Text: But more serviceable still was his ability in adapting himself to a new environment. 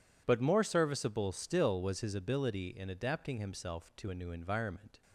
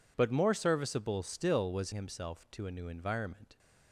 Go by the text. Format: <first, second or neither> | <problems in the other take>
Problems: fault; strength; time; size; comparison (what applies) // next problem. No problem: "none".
first | skips "his ability in adapting"; at 1.9 s